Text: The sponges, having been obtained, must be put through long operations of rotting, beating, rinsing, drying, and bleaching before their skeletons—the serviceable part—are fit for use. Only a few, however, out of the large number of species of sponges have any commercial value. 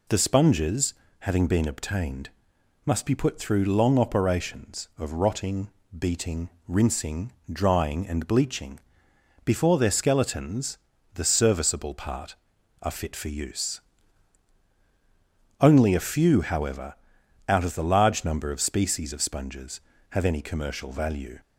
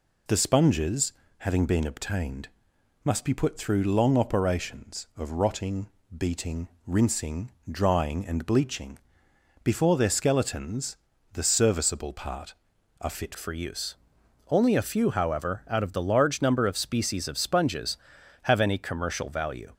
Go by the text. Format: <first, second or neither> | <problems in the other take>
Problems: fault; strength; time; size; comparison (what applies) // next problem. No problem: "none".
first | pauses between "bleaching" and "before"; noticeable; at 8.9 s; 0.64 s long; noticeable in the first // changes voice at "for"; from 13.3 s on; 6.4 s long